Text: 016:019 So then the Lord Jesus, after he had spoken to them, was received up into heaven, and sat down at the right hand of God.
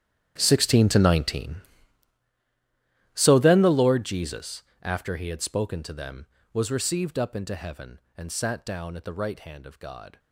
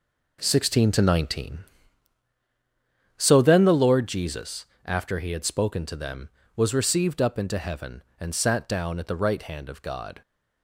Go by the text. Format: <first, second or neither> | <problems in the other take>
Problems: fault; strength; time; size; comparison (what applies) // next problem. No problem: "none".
second | gets quieter; strong; throughout; 18.5 dB